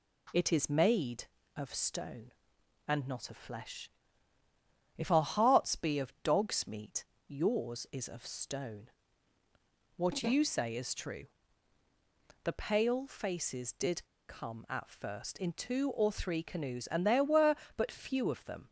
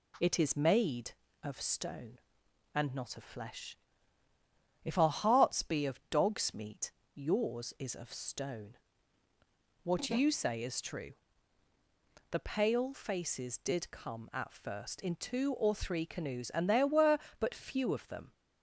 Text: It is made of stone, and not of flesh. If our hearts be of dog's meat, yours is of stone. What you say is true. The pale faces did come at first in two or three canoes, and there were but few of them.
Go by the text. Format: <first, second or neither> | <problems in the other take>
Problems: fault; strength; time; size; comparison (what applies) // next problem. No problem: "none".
second | pauses between "did" and "come"; slight; at 14.0 s; 0.24 s long